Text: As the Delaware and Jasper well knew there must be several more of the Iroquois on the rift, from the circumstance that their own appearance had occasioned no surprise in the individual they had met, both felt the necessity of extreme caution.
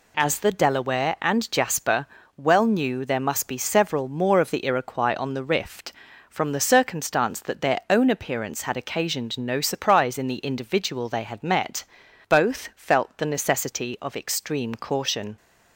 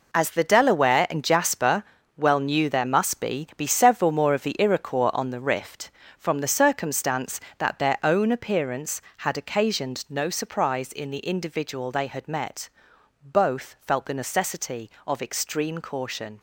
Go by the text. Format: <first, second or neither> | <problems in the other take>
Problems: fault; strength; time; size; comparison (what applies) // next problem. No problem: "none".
first | pauses between "Jasper" and "well"; slight; at 1.8 s; 0.32 s long; slight in the first // says "be" twice; at 3.5 s